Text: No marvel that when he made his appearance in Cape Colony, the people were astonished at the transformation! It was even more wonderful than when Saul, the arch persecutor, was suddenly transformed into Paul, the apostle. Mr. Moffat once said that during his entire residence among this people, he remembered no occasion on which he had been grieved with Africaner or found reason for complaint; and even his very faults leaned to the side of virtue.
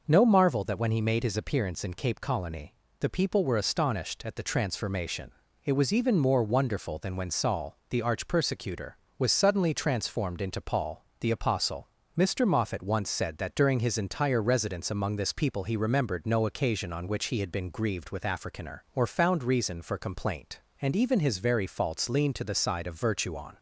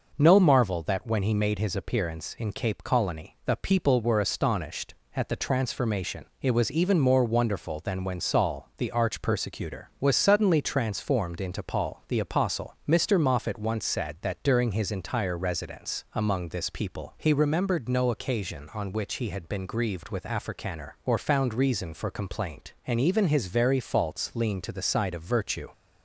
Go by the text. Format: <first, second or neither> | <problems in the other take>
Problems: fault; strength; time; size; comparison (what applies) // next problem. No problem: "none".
second | goes on to say "On"; slight; from 23.3 s on; 0.22 s long